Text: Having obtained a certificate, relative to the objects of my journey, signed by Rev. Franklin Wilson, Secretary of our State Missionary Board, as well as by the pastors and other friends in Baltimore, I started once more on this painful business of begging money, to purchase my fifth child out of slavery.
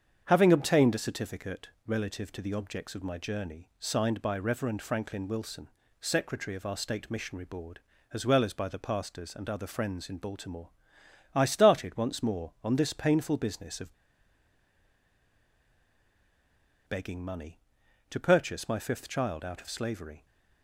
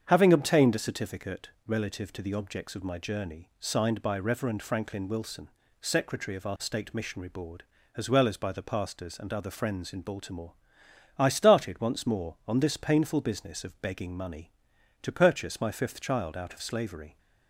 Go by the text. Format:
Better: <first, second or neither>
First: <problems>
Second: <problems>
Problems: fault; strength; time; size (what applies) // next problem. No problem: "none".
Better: second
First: starts louder than the rest; strong; until 1.2 s; 7.5 dB // pauses between "of" and "begging"; strong; at 13.9 s; 2.9 s long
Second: starts louder than the rest; strong; until 1.0 s; 7.5 dB